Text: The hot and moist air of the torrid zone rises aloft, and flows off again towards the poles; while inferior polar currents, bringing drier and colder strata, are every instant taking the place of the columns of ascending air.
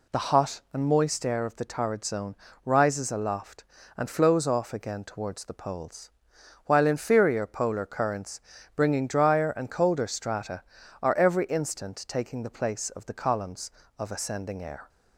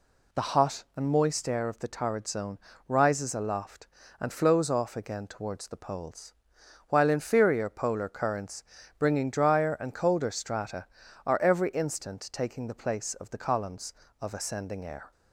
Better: neither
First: pauses between "zone" and "rises"; slight; at 2.3 s; 0.30 s long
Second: pauses between "zone" and "rises"; slight; at 2.5 s; 0.30 s long

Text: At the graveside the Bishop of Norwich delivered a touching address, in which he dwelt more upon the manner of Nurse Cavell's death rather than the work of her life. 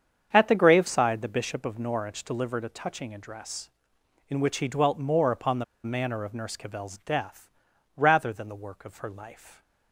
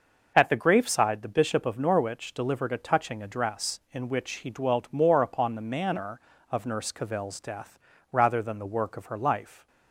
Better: second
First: starts louder than the rest; strong; until 1.3 s; 7.5 dB // pauses between "the" and "manner"; slight; at 5.6 s; 0.19 s long // pauses between "death" and "rather"; noticeable; at 7.4 s; 0.48 s long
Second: pauses between "death" and "rather"; slight; at 7.7 s; 0.32 s long

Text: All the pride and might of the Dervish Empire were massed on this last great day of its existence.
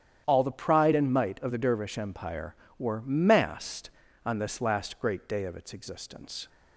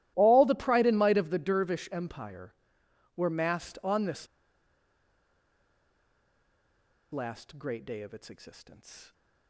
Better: first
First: starts louder than the rest; strong; until 1.2 s; 10 dB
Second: starts louder than the rest; strong; until 1.1 s; 15 dB // pauses between "this" and "last"; strong; at 4.2 s; 2.8 s long

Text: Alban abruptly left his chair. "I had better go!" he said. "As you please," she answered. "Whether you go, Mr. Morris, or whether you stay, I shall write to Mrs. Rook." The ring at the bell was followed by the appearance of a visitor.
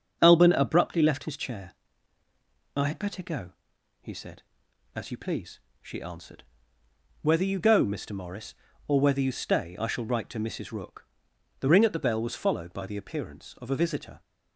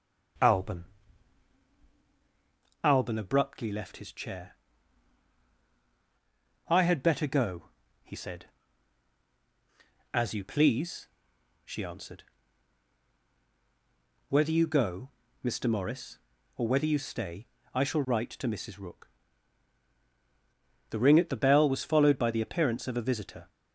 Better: first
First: starts louder than the rest; until 1.2 s; 6.5 dB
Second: starts louder than the rest; until 3.3 s; 6.5 dB // says "Alban" twice; at 2.8 s

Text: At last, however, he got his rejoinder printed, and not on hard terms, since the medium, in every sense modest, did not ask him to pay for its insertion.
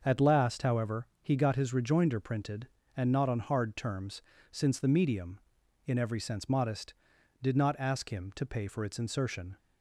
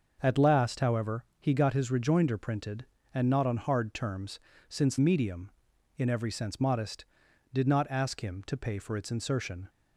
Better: first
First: starts louder than the rest; until 1.0 s; 6 dB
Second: starts louder than the rest; until 1.2 s; 6 dB // skips "the"; at 4.9 s

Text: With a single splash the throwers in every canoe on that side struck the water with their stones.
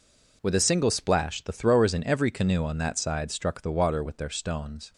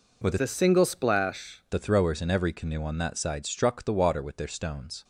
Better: first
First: none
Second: changes voice from "a" to "splash"; from 0.4 to 1.6 s; 1.2 s long

